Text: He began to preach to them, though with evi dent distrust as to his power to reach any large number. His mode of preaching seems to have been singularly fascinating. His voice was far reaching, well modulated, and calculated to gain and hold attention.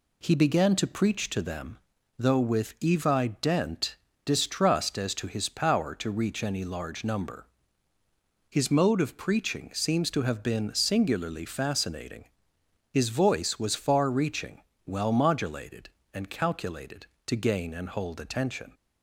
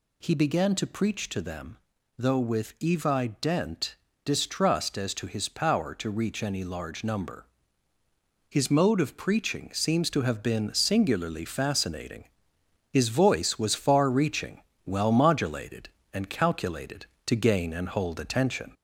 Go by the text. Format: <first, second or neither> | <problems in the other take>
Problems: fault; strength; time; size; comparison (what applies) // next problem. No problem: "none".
first | gets louder; slight; throughout; 2.5 dB // pauses between "dent" and "distrust"; slight; at 3.9 s; 0.28 s long; slight in the first